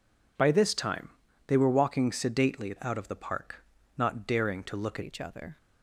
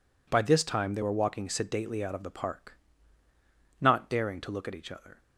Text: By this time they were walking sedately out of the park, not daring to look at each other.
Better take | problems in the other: second | pauses between "time" and "they"; at 1.0 s; 0.38 s long // changes voice at "each"; from 5.0 s on; 0.5 s long

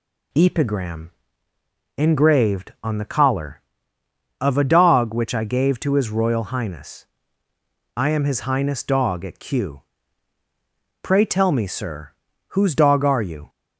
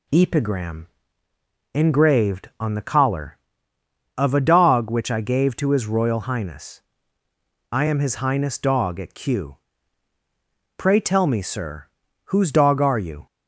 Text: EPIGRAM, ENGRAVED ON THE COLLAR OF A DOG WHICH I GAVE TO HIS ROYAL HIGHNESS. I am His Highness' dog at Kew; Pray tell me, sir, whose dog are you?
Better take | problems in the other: neither | none

